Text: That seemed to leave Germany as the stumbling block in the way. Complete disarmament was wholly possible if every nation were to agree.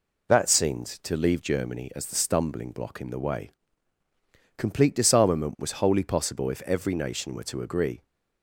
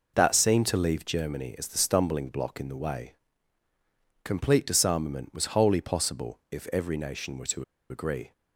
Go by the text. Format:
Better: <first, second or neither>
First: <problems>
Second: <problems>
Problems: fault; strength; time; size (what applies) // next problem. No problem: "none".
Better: first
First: none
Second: pauses between "to" and "agree"; slight; at 7.6 s; 0.25 s long